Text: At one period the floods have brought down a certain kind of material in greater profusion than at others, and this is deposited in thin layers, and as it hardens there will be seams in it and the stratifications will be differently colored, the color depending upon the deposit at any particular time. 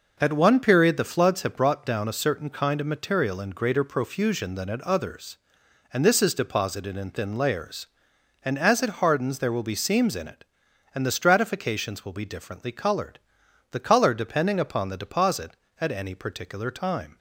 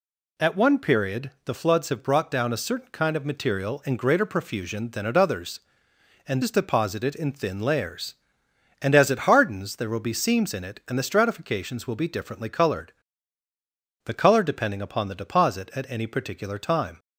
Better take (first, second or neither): first